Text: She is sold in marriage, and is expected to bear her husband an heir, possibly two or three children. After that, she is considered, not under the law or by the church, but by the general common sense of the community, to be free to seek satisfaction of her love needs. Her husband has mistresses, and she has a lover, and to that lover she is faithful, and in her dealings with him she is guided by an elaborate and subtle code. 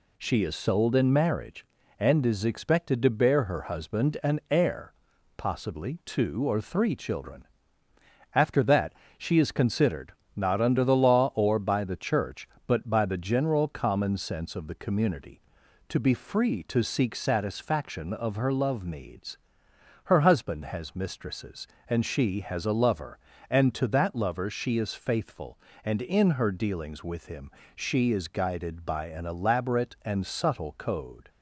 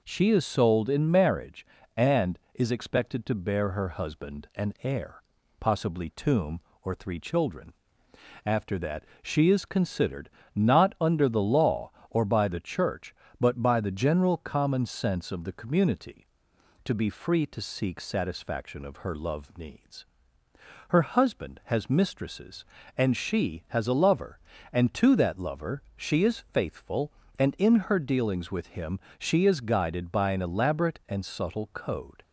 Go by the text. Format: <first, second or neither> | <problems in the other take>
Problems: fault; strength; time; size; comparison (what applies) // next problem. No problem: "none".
first | says "tomb" for "two"; at 6.0 s // pauses between "him" and "she"; slight; at 28.9 s; 0.18 s long; slight in the first